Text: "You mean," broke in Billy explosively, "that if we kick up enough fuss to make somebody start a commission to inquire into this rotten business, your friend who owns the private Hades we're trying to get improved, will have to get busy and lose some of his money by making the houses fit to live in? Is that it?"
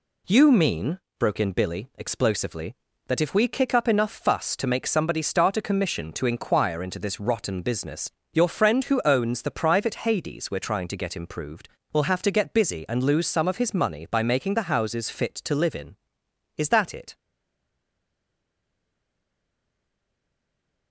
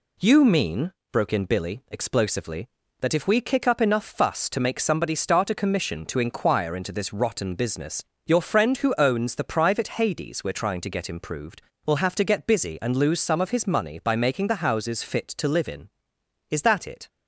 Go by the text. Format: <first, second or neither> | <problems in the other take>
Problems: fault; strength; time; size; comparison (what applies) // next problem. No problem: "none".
second | stays silent after the last word; strong; from 17.1 s on; 3.8 s long